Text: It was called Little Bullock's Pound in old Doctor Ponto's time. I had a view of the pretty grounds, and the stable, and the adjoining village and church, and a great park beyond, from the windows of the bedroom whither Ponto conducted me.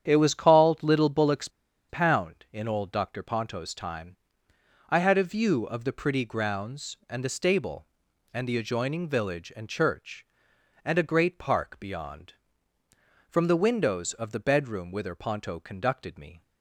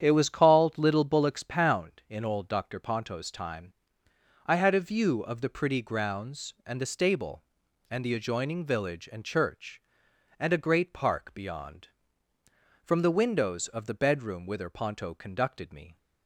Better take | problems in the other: second | starts louder than the rest; strong; until 1.0 s; 8.5 dB; strong in the second // pauses between "Bullock's" and "Pound"; at 1.4 s; 0.41 s long

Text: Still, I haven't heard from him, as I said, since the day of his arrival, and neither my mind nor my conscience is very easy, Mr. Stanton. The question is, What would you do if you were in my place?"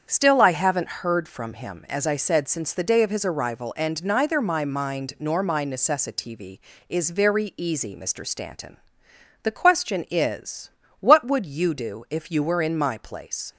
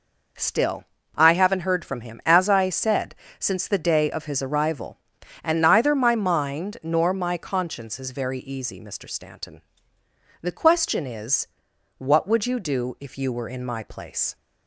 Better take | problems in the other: second | starts louder than the rest; strong; until 1.0 s; 7.5 dB // says "necessitv" for "conscience"; at 5.6 s

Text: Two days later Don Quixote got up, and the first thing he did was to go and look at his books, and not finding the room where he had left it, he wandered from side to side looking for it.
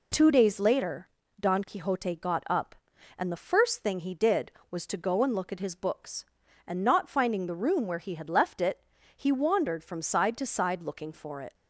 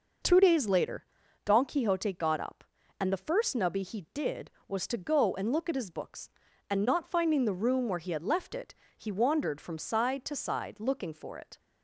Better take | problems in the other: first | pauses between "later" and "Don"; at 1.0 s; 0.40 s long; slight in the first // says "nubby" for "thing"; at 3.5 s

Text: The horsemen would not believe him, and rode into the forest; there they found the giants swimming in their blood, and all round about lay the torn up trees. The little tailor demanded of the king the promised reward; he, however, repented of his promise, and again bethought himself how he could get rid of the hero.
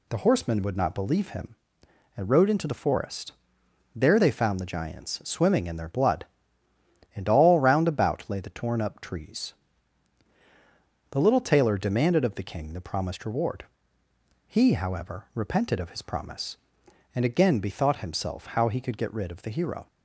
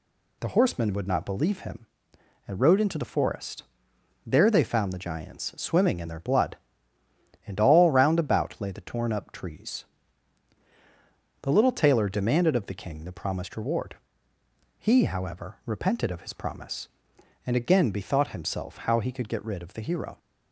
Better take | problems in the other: neither | none

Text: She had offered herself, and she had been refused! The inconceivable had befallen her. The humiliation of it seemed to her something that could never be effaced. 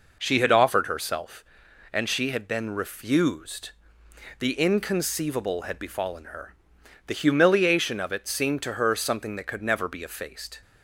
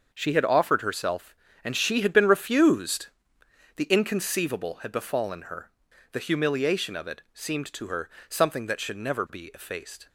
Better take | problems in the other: first | starts louder than the rest; until 1.1 s; 6.5 dB // pauses between "her" and "something"; slight; at 8.0 s; 0.18 s long // says "should" for "could"; at 8.7 s

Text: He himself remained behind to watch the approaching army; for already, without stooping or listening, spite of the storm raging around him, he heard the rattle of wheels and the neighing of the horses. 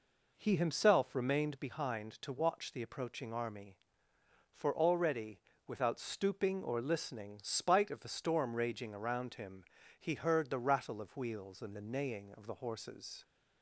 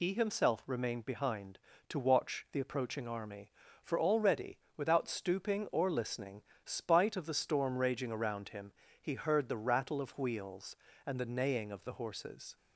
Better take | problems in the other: first | loses the start of "He"; at 0.0 s; 80 ms

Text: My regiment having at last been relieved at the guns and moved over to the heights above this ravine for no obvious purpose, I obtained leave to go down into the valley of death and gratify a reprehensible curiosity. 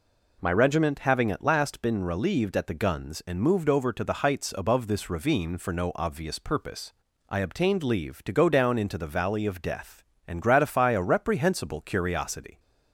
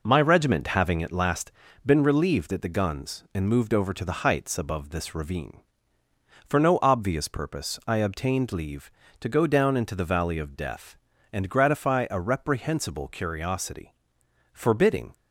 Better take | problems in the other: first | pauses between "last" and "been"; slight; at 1.5 s; 0.34 s long // goes on to say "Forbidding"; noticeable; from 14.5 s on; 0.62 s long

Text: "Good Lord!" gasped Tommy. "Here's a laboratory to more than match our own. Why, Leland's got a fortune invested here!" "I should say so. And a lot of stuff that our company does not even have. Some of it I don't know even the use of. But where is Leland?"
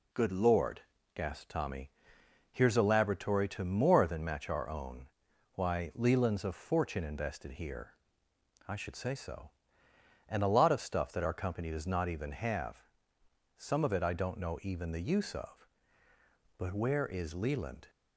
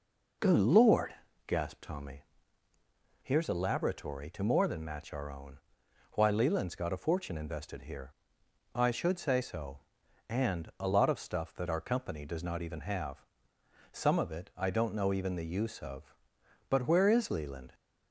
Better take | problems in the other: second | skips "got"; at 6.4 s

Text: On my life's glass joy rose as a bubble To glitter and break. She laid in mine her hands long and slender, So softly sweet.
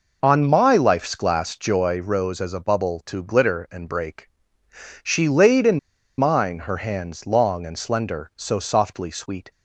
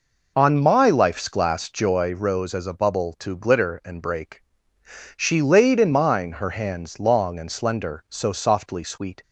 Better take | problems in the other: second | pauses between "in" and "mine"; at 5.7 s; 0.40 s long

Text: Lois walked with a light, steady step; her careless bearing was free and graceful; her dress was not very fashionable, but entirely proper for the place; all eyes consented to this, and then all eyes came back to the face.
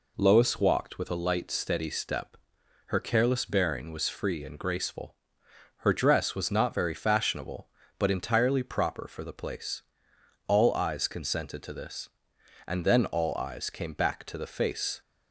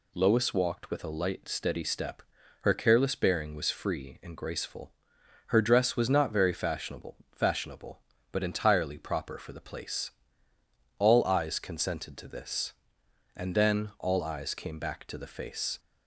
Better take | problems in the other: first | says "fashionable" twice; at 7.3 s

